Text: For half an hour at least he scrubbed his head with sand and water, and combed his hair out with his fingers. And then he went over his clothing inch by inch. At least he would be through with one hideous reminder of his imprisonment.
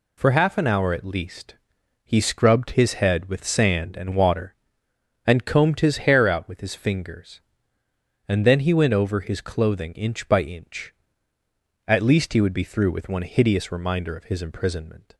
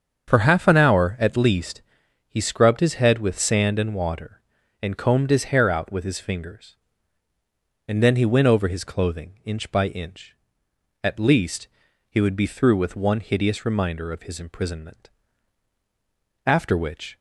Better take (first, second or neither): first